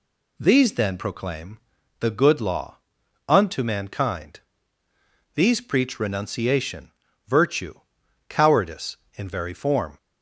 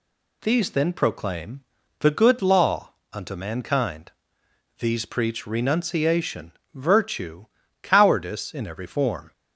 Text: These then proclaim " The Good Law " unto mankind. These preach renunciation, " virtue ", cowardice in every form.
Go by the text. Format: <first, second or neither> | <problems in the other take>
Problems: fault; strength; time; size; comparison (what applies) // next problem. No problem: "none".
second | says "very" for "every"; at 9.2 s